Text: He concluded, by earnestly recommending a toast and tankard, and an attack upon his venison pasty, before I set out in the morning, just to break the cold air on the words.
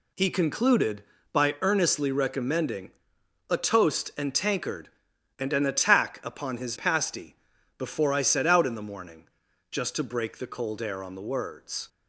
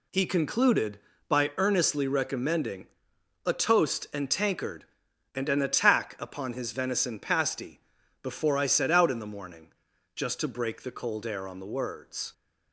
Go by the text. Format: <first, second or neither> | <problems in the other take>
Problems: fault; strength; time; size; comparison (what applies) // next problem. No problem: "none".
second | pauses between "recommending" and "a"; noticeable; at 2.9 s; 0.58 s long; noticeable in the second // skips "venison"; at 6.7 s